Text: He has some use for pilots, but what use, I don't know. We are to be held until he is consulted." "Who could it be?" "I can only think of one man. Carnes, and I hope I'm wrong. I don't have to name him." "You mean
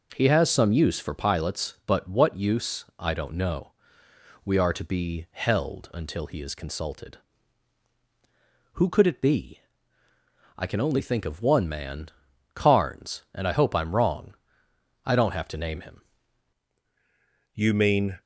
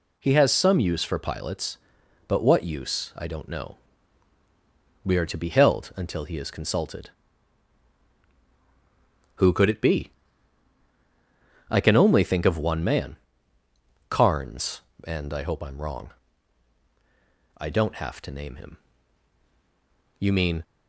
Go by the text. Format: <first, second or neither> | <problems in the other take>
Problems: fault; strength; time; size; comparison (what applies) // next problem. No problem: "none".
second | changes voice at "You"; from 17.5 s on; 0.7 s long